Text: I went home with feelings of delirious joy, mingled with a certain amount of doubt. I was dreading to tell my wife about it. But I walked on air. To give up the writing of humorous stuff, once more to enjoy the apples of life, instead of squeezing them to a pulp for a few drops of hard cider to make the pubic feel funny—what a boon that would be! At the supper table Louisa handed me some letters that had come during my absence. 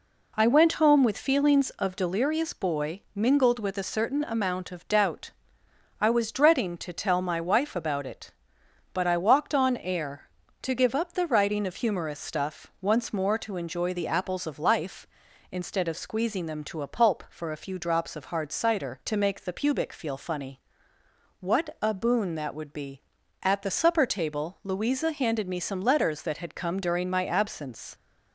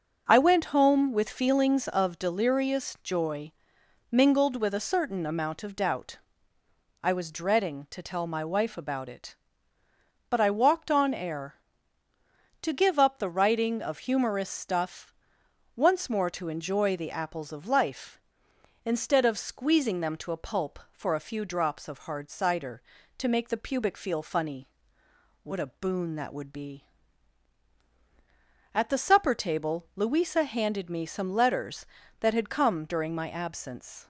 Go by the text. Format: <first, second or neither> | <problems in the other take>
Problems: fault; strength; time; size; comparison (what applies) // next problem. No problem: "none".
second | says "boy" for "joy"; at 2.5 s